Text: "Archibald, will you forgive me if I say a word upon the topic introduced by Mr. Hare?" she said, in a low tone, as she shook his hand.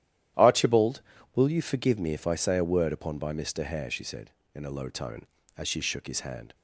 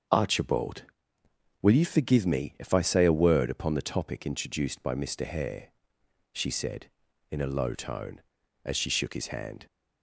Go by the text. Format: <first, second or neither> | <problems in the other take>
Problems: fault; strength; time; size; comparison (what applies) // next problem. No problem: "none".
second | starts louder than the rest; strong; until 1.7 s; 12 dB; also in the second // skips "the topic introduced"; at 3.1 s